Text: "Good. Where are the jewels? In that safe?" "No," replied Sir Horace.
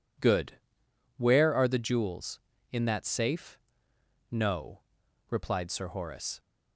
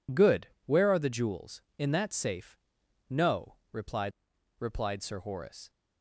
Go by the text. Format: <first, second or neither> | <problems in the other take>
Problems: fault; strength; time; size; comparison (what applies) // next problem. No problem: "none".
first | says "replied" twice; at 4.5 s